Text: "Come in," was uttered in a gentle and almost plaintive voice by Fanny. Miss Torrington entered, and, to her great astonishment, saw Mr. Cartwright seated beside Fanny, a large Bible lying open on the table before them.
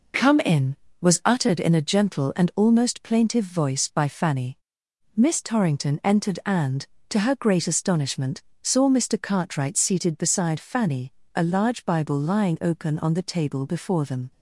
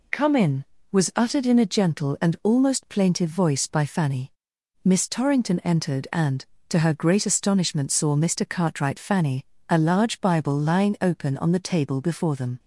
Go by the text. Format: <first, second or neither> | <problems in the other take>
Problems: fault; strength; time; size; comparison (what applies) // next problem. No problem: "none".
first | skips "seated beside"; at 8.9 s